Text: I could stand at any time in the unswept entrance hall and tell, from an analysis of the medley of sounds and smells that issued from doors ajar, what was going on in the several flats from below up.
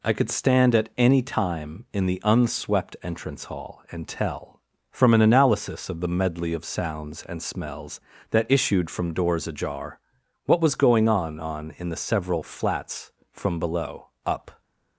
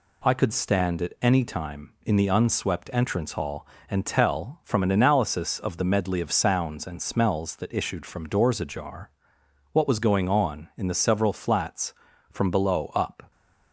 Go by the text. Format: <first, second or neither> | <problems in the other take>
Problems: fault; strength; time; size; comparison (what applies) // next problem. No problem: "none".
second | says "on" twice; at 11.4 s // pauses between "below" and "up"; slight; at 14.0 s; 0.16 s long